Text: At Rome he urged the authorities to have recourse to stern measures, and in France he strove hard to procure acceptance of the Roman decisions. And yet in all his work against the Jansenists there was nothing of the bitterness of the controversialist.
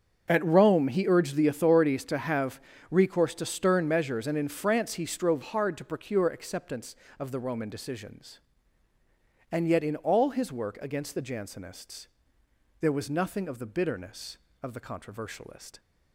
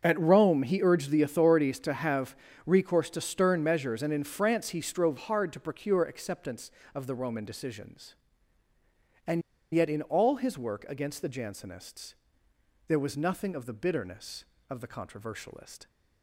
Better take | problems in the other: first | starts louder than the rest; until 1.0 s; 7 dB; also in the first // pauses between "have" and "recourse"; slight; at 2.3 s; 0.30 s long; slight in the first // pauses between "And" and "yet"; slight; at 9.4 s; 0.30 s long // pauses between "Jansenists" and "there"; noticeable; at 12.1 s; 0.72 s long; noticeable in the first

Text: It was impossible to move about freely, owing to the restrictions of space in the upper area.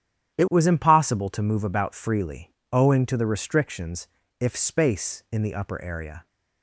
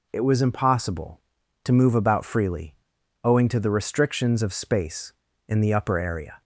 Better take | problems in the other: second | starts louder than the rest; strong; until 1.4 s; 10.5 dB // says "if" for "of"; at 4.3 s

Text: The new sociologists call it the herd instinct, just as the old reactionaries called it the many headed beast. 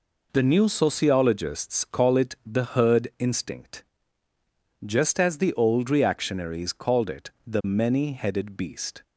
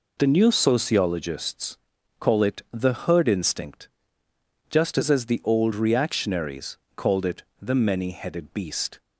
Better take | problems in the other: first | pauses between "sociologists" and "call"; at 1.7 s; 0.40 s long // says "as" twice; at 5.1 s // pauses between "reactionaries" and "called"; slight; at 6.7 s; 0.16 s long // pauses between "it" and "the"; slight; at 7.4 s; 0.18 s long; slight in the first

